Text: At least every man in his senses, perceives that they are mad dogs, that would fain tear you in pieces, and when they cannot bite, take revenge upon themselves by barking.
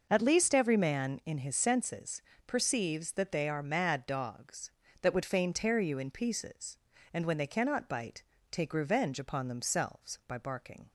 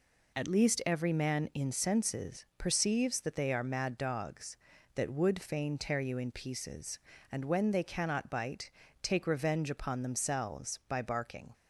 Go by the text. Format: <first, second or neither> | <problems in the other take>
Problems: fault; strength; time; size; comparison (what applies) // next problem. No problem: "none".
first | skips "his"; at 1.7 s